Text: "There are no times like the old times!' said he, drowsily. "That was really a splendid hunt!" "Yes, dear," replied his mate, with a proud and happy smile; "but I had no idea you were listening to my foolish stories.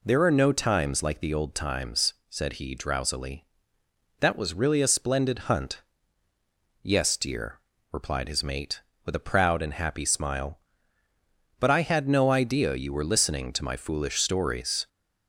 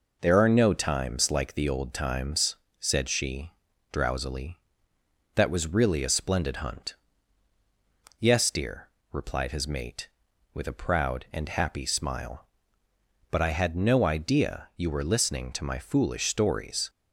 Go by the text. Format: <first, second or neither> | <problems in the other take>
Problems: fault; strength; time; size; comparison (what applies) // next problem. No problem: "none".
first | says "she" for "he"; at 3.0 s